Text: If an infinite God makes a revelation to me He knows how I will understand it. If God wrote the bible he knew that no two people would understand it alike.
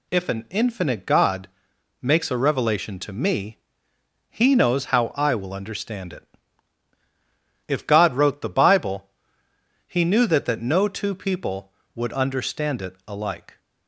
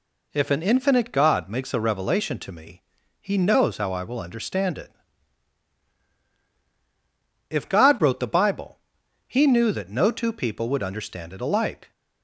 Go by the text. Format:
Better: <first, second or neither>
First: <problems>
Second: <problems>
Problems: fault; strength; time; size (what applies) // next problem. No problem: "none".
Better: second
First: pauses between "God" and "makes"; noticeable; at 1.4 s; 0.52 s long // pauses between "me" and "He"; noticeable; at 3.5 s; 0.72 s long // pauses between "bible" and "he"; noticeable; at 9.0 s; 0.80 s long // says "that" twice; at 10.4 s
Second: pauses between "me" and "He"; at 2.8 s; 0.38 s long // pauses between "bible" and "he"; noticeable; at 8.7 s; 0.50 s long